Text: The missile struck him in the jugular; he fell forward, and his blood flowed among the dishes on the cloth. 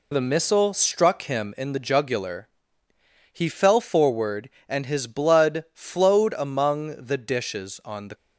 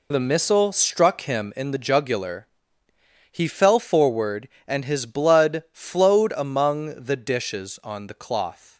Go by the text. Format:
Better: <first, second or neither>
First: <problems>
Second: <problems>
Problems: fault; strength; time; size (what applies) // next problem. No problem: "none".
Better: second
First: stops before "cloth"; at 8.1 s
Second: none